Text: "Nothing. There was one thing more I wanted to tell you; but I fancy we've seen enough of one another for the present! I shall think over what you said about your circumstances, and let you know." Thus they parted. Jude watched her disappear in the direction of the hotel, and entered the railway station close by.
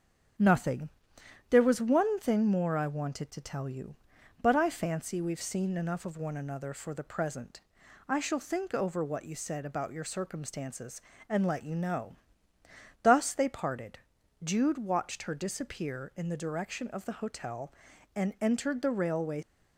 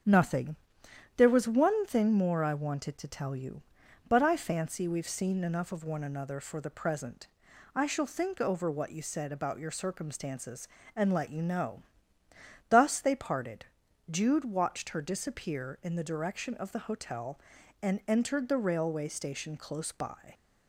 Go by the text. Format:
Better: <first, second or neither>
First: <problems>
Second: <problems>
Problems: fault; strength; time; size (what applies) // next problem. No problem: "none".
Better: second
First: starts louder than the rest; until 1.9 s; 7 dB // stops before "station close by"; at 19.4 s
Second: starts louder than the rest; until 1.6 s; 7 dB